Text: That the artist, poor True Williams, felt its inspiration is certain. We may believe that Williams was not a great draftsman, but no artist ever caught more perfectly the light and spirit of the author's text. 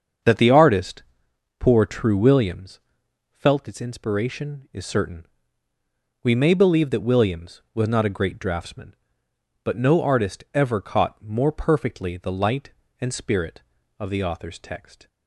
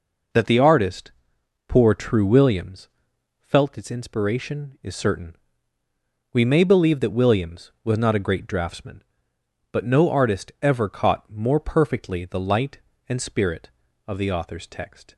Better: second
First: starts louder than the rest; until 1.3 s; 7 dB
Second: none

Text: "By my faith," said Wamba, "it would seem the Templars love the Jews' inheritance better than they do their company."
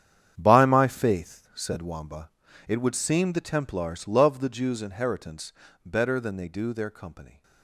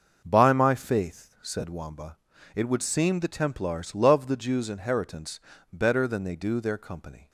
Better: second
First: gets quieter; strong; throughout; 13.5 dB // starts louder than the rest; strong; until 1.3 s; 9 dB // pauses between "inheritance" and "better"; slight; at 5.5 s; 0.32 s long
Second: starts louder than the rest; noticeable; until 1.2 s; 6 dB // pauses between "inheritance" and "better"; slight; at 5.3 s; 0.32 s long

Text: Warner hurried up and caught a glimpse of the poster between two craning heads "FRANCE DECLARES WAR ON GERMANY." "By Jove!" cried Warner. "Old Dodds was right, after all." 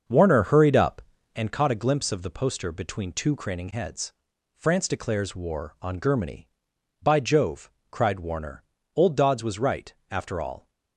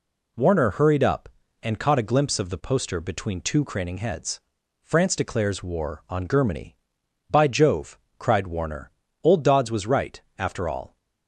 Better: second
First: starts louder than the rest; until 1.5 s; 6.5 dB // pauses between "heads" and "FRANCE"; at 4.1 s; 0.42 s long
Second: pauses between "heads" and "FRANCE"; at 4.4 s; 0.42 s long

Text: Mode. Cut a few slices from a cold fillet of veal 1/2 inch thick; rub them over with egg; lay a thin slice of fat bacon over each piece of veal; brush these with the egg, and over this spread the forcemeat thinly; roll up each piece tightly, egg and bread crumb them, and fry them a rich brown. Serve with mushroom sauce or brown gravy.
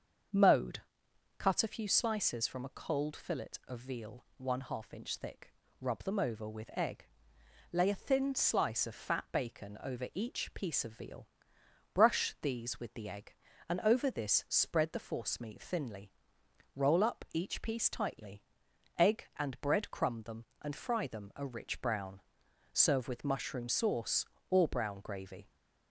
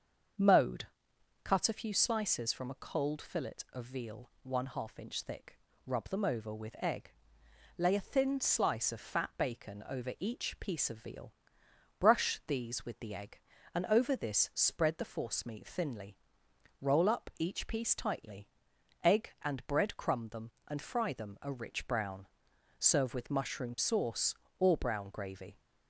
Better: neither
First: starts louder than the rest; until 1.9 s; 6.5 dB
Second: starts louder than the rest; until 1.9 s; 6.5 dB

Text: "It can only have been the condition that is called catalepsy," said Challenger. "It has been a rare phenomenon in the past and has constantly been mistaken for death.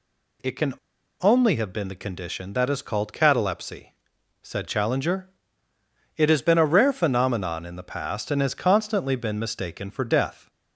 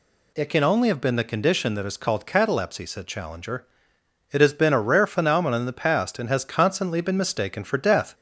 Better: second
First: pauses between "can" and "only"; noticeable; at 0.7 s; 0.49 s long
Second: none

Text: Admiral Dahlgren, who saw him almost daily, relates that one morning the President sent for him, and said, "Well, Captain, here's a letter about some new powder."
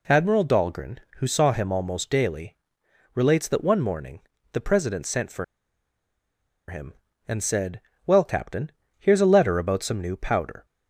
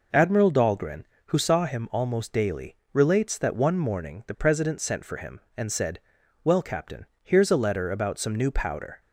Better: second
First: pauses between "morning" and "the"; slight; at 4.1 s; 0.32 s long // pauses between "for" and "him"; strong; at 5.4 s; 1.2 s long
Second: none

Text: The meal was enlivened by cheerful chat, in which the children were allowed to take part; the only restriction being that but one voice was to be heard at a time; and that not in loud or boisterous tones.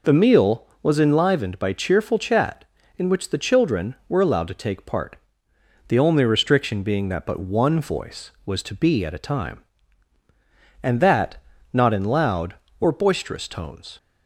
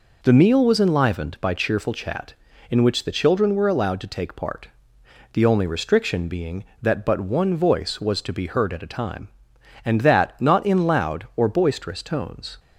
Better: second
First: skips "heard"; at 9.0 s // pauses between "that" and "not"; slight; at 11.3 s; 0.36 s long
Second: none

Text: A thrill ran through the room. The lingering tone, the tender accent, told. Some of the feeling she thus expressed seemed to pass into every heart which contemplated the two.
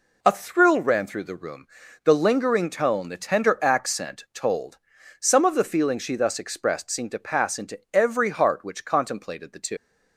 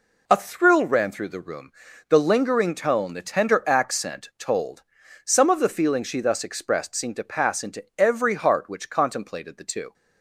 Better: second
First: leaves "two" unfinished; at 9.7 s; 115 ms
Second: none

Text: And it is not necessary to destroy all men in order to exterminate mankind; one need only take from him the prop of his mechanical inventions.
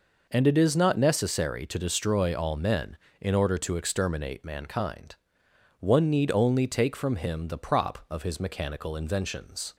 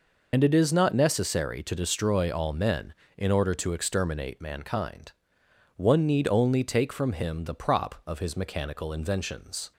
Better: first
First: none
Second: loses the start of "And"; at 0.3 s; 70 ms

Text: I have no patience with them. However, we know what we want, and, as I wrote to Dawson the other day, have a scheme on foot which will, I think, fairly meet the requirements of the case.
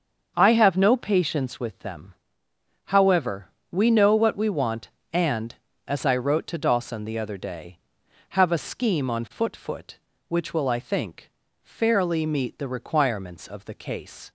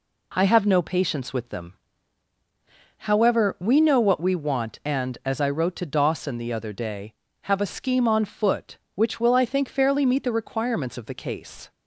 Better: second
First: starts louder than the rest; until 1.3 s; 6.5 dB // says "foot" twice; at 9.5 s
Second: none

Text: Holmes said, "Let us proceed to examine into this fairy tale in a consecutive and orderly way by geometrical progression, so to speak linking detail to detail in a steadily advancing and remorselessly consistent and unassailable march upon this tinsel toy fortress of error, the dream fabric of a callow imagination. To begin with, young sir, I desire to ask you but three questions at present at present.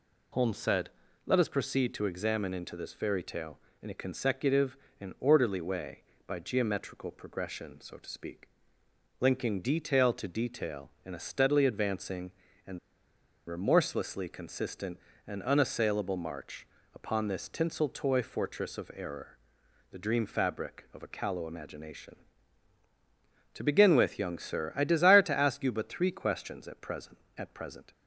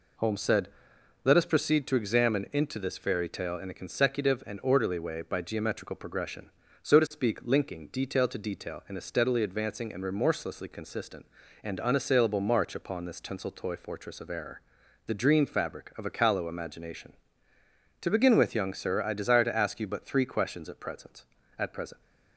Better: second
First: pauses between "speak" and "linking"; noticeable; at 8.4 s; 0.72 s long // pauses between "and" and "remorselessly"; noticeable; at 12.7 s; 0.70 s long // pauses between "march" and "upon"; slight; at 16.6 s; 0.26 s long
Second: none

